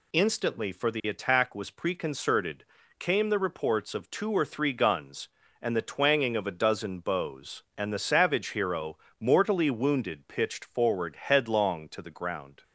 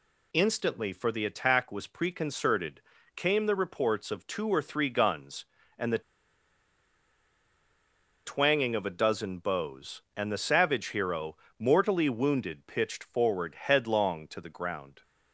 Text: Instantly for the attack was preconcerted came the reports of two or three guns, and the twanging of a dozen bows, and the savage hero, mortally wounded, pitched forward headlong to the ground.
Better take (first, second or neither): first